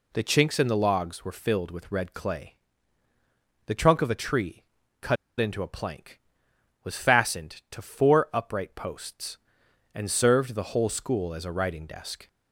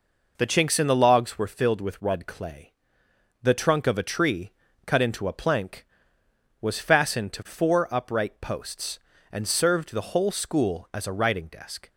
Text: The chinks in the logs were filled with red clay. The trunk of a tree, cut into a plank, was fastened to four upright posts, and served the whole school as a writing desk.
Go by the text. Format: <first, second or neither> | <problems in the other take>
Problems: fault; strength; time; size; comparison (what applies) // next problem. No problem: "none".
second | pauses between "cut" and "into"; slight; at 5.1 s; 0.23 s long